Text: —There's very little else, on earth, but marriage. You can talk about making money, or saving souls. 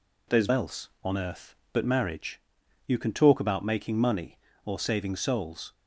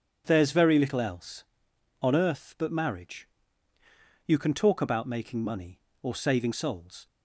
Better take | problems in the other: second | skips "very little"; at 0.4 s

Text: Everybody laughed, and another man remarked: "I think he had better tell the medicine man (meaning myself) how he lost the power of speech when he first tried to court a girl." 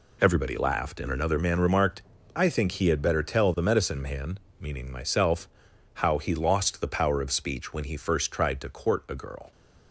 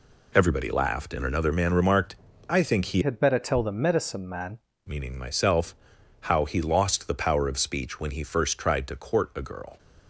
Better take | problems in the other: first | changes voice from "had" to "man"; from 3.0 to 4.5 s; 1.5 s long

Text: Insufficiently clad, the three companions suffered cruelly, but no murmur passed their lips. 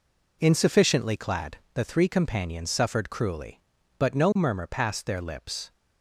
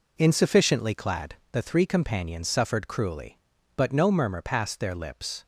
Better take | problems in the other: neither | none

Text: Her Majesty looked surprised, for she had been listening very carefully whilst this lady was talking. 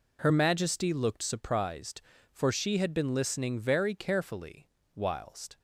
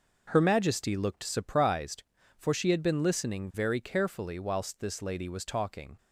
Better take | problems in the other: second | pauses between "carefully" and "whilst"; slight; at 4.6 s; 0.26 s long // stops before "this lady was talking"; at 5.5 s

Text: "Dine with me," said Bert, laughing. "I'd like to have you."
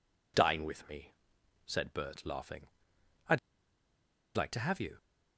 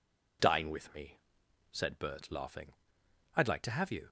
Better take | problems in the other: second | pauses between "I'd" and "like"; at 3.3 s; 0.98 s long

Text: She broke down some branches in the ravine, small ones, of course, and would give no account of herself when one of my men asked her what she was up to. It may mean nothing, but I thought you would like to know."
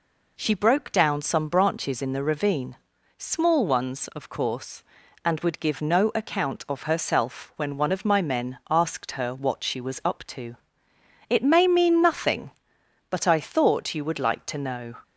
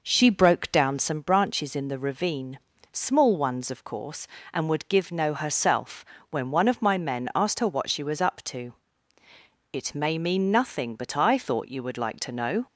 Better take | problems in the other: first | skips "account of"; at 5.3 s // pauses between "herself" and "when"; slight; at 6.0 s; 0.28 s long

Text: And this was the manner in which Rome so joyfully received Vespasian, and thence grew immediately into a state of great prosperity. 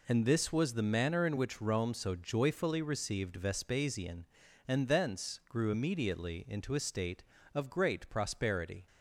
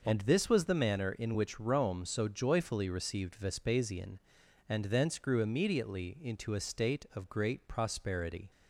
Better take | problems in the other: neither | none

